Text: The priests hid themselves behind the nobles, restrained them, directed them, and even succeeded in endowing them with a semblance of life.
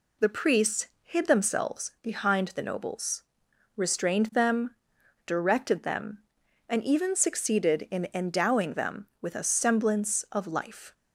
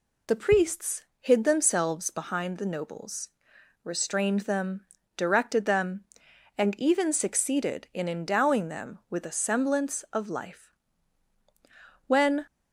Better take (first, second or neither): first